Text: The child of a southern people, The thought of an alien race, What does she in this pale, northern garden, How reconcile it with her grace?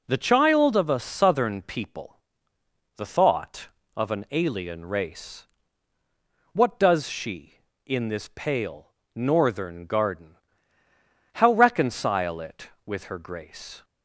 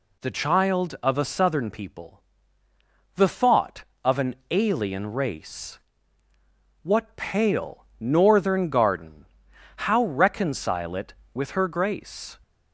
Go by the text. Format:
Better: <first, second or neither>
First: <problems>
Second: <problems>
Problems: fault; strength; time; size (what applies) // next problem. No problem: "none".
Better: first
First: none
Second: pauses between "an" and "alien"; slight; at 4.3 s; 0.16 s long // skips "does she in this"; at 7.1 s